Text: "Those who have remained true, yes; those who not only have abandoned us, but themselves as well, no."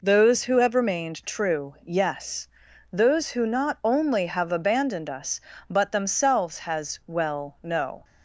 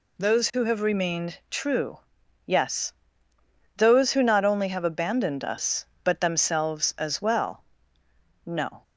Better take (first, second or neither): second